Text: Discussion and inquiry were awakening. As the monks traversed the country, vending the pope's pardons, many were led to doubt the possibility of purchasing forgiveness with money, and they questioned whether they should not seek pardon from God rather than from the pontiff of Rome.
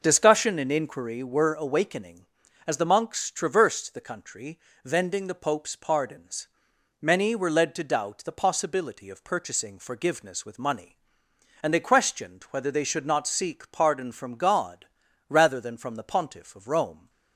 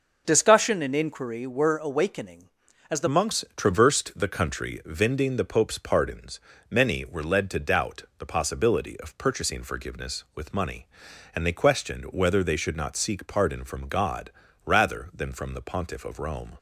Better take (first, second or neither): first